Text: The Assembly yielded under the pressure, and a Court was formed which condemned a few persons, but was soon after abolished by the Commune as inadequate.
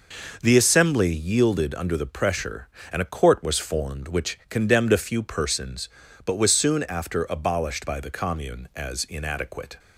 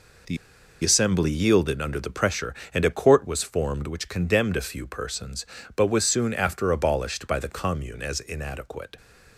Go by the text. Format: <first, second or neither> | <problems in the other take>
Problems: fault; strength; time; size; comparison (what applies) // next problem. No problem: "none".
first | pauses between "The" and "Assembly"; noticeable; at 0.3 s; 0.47 s long